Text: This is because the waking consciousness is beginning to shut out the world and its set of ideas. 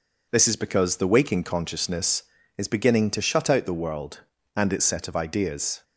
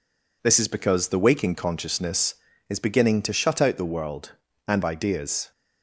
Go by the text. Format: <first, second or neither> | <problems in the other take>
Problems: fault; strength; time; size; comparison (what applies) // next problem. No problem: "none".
first | skips "its set of"; at 4.8 s